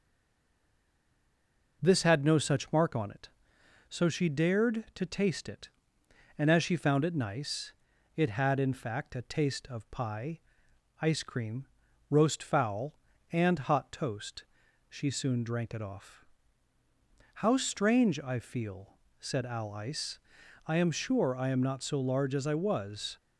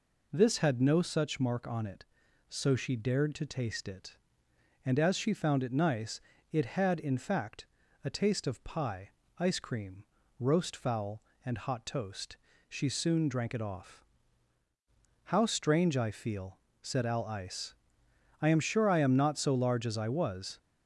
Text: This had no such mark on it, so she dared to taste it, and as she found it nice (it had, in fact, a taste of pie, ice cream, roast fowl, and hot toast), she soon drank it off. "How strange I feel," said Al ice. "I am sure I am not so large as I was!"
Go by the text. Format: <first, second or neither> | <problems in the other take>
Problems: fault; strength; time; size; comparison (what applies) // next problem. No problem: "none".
second | stays silent before the first word; noticeable; until 1.8 s; 1.8 s long